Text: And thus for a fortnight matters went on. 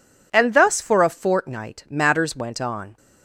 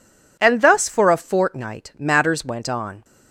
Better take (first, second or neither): neither